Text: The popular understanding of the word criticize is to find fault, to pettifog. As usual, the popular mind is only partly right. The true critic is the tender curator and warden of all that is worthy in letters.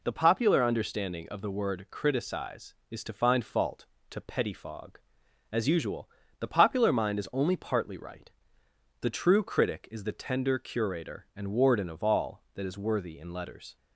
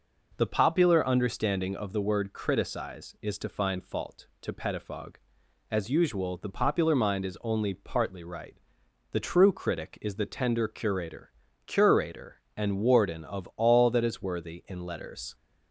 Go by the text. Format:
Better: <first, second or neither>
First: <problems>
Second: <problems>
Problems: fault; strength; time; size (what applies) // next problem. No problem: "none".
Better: first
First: none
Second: says "curator" twice; at 11.6 s